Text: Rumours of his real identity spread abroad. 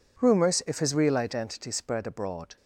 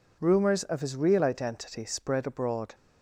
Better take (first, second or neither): second